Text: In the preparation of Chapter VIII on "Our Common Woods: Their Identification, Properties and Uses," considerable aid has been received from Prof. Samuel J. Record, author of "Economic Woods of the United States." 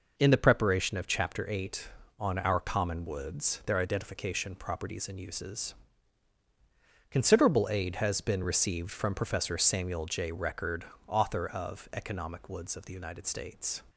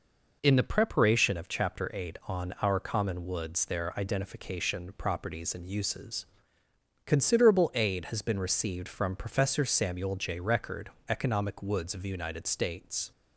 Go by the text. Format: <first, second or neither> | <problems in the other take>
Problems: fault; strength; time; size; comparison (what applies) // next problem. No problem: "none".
first | skips "author of"; at 11.0 s